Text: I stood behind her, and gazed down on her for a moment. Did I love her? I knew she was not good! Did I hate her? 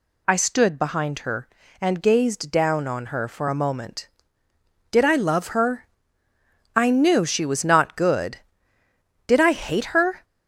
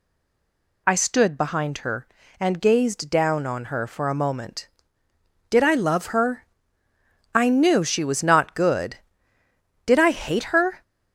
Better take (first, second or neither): first